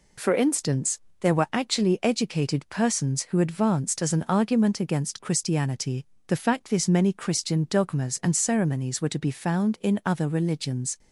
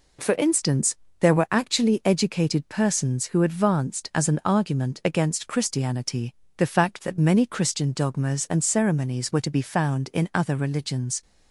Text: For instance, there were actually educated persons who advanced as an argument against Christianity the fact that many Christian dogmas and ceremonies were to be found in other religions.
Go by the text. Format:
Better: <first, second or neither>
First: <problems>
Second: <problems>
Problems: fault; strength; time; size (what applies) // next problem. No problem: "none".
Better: second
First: pauses between "Christianity" and "the"; slight; at 6.0 s; 0.20 s long // says "this" for "that"; at 6.7 s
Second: pauses between "Christianity" and "the"; slight; at 6.3 s; 0.24 s long